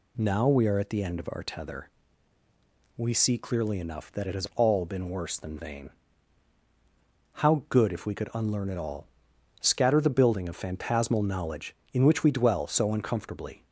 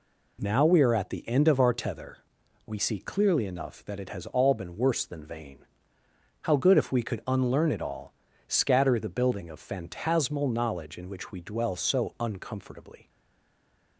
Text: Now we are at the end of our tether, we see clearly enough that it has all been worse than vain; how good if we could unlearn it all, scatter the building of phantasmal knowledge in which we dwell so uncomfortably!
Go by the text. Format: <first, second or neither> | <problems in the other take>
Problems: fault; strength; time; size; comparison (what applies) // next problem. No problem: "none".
first | stays silent after the last word; slight; from 13.0 s on; 0.9 s long